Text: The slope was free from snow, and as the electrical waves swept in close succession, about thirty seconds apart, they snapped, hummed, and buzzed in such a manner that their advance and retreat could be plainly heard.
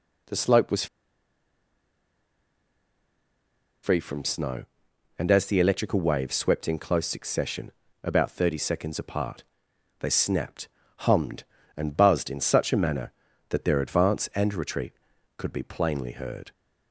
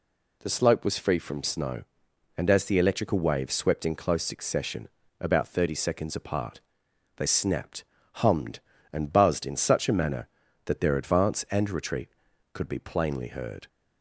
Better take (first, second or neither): second